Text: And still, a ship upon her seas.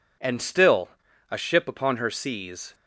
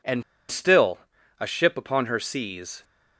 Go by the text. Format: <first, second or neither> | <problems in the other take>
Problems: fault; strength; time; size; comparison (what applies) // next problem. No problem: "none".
first | pauses between "And" and "still"; slight; at 0.2 s; 0.28 s long